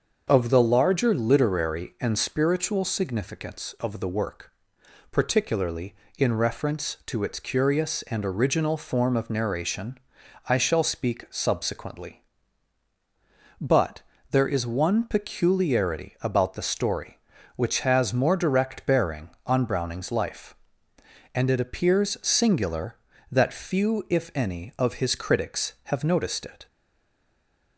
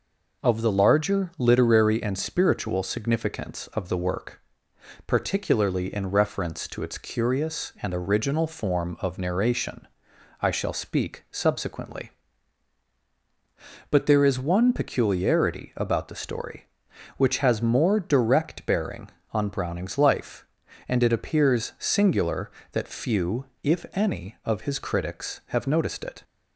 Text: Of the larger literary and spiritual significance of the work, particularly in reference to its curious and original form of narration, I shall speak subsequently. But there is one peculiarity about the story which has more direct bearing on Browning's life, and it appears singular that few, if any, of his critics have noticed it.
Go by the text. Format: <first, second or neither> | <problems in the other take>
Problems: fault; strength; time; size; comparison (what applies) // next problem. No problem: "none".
second | starts louder than the rest; until 1.2 s; 6.5 dB // pauses between "But" and "there"; slight; at 14.0 s; 0.28 s long // stays silent after the last word; from 26.6 s on; 1.1 s long